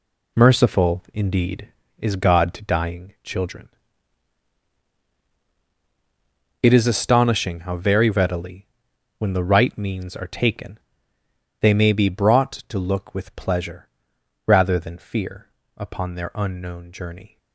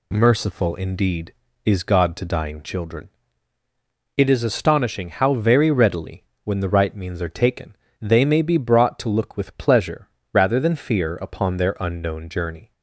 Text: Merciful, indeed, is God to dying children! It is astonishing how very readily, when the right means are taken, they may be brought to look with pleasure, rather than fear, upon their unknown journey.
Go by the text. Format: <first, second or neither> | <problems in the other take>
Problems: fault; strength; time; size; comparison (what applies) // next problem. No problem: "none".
second | gets quieter; strong; throughout; 8 dB